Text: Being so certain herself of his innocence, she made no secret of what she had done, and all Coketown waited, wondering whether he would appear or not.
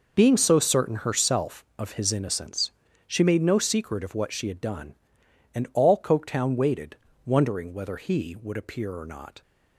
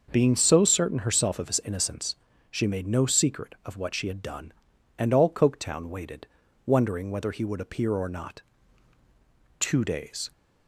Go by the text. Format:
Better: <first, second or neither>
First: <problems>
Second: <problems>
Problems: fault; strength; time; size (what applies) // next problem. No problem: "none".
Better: first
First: none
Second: starts louder than the rest; noticeable; until 1.1 s; 6 dB // goes on to say "Two days"; noticeable; from 9.5 s on; 0.72 s long